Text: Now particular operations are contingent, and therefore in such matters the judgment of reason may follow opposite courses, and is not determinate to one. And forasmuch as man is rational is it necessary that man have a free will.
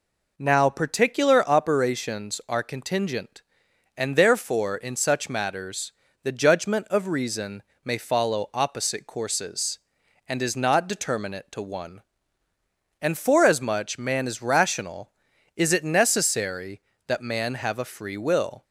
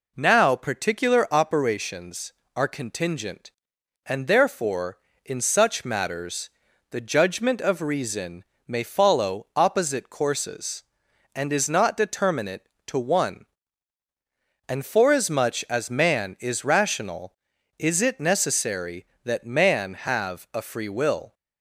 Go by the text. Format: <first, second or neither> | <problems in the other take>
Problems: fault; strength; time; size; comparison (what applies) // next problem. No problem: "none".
second | pauses between "matters" and "the"; slight; at 5.9 s; 0.32 s long; also in the second // pauses between "reason" and "may"; slight; at 7.6 s; 0.22 s long; slight in the second // skips "as"; at 13.9 s